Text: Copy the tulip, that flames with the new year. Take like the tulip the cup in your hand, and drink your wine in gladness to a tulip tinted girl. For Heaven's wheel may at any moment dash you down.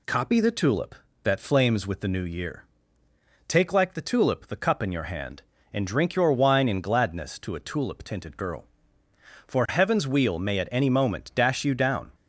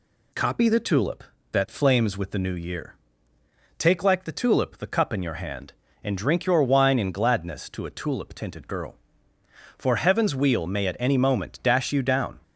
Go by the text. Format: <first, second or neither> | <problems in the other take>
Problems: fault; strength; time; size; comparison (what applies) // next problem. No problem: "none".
neither | none